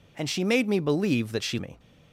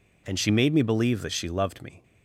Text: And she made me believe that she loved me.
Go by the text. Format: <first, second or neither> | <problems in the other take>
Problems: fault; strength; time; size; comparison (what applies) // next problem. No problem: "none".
second | skips "loved"; at 1.5 s